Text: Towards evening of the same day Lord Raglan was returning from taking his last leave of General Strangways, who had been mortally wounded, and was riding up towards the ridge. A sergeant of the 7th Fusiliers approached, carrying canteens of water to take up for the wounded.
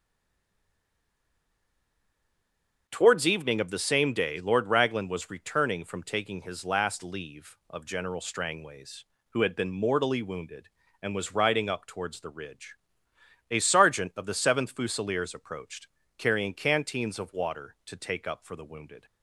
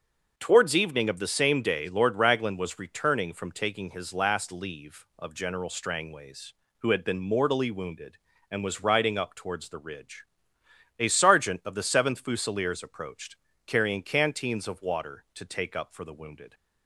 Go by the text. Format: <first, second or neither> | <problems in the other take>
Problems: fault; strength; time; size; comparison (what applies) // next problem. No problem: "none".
second | stays silent before the first word; strong; until 2.8 s; 2.8 s long // starts louder than the rest; until 3.8 s; 6 dB; also in the second